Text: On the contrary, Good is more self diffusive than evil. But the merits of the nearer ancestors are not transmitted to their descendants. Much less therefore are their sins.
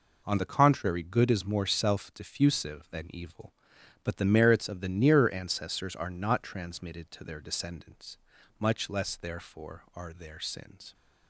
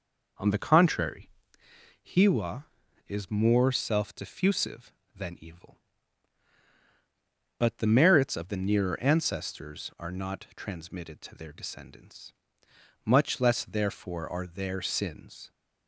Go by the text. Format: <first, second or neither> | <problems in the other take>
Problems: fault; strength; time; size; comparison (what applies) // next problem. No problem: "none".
first | says "Hiwa" for "Good"; at 2.0 s